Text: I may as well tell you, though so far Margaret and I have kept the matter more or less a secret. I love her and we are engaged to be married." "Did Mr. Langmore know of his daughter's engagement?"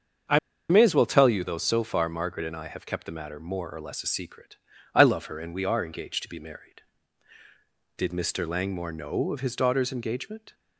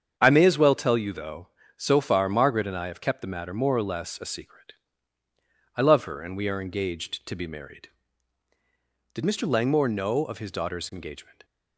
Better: second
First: starts louder than the rest; until 1.6 s; 7 dB // pauses between "I" and "may"; slight; at 0.3 s; 0.30 s long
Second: starts louder than the rest; strong; until 1.1 s; 7.5 dB

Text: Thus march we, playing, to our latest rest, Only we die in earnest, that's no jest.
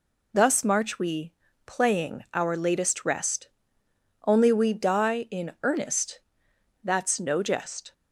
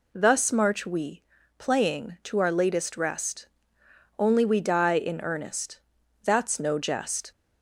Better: second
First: skips "to"; at 2.2 s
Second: none

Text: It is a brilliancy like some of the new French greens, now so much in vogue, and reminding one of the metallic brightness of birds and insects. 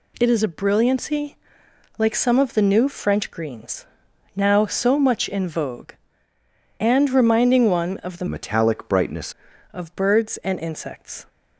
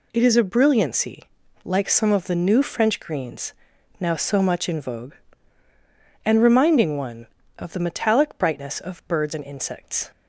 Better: second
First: pauses between "brilliancy" and "like"; noticeable; at 1.3 s; 0.62 s long // changes voice from "metallic" to "brightness"; from 8.2 to 9.3 s; 1.1 s long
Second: pauses between "brilliancy" and "like"; at 1.2 s; 0.40 s long

